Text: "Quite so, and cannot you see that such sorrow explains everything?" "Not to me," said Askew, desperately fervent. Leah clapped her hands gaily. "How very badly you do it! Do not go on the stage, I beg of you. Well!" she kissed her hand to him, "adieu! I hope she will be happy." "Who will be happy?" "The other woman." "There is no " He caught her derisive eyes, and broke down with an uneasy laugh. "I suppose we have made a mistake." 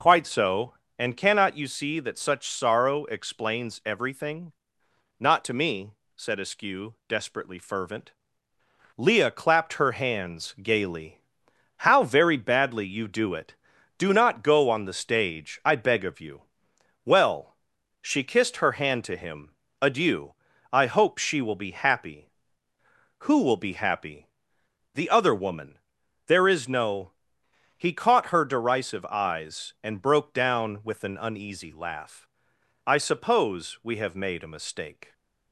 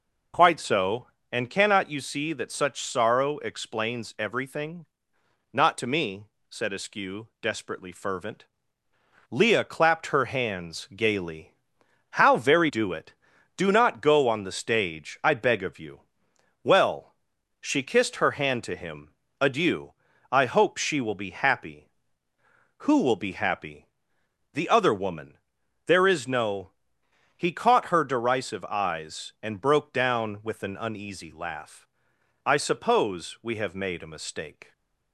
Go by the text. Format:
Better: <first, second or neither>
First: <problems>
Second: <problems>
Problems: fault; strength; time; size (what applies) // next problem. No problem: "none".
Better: first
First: none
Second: skips "badly you"; at 12.6 s // stays silent after the last word; slight; from 34.6 s on; 0.5 s long